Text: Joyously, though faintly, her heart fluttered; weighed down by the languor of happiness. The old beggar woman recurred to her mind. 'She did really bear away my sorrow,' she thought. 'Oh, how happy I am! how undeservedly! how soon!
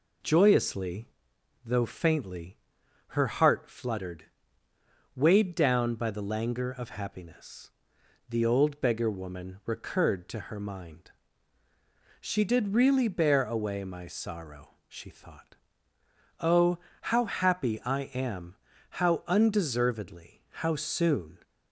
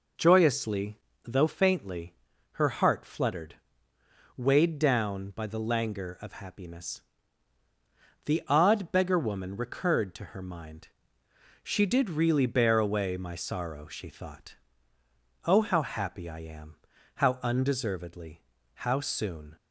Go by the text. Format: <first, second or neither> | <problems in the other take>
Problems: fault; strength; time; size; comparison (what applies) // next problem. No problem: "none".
first | says "odd" for "old"; at 8.4 s